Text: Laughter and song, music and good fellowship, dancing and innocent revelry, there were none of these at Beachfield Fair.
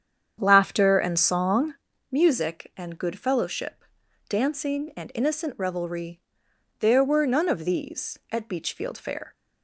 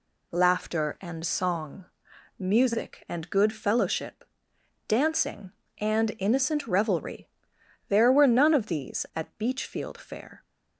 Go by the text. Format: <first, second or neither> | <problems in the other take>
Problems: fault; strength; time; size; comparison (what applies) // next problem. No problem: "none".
second | starts louder than the rest; strong; until 1.9 s; 8 dB